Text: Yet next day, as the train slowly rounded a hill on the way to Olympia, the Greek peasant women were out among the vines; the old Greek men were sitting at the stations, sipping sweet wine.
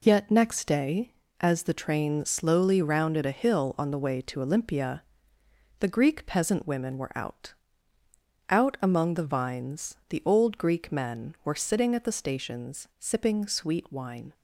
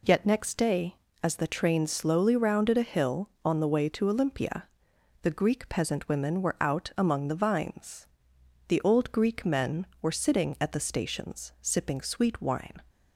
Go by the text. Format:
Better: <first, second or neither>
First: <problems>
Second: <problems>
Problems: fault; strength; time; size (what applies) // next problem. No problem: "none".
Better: second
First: says "out" twice; at 8.4 s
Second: none